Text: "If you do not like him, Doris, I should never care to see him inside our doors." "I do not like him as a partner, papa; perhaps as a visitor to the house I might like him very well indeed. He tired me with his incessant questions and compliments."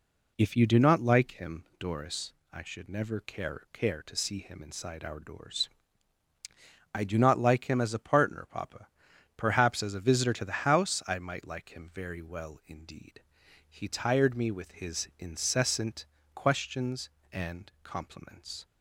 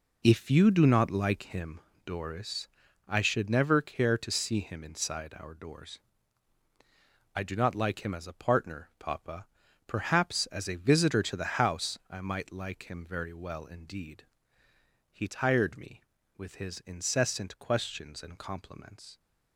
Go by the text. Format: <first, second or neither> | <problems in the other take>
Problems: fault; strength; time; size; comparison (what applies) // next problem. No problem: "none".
second | says "care" twice; at 3.7 s // pauses between "incessant" and "questions"; slight; at 16.0 s; 0.28 s long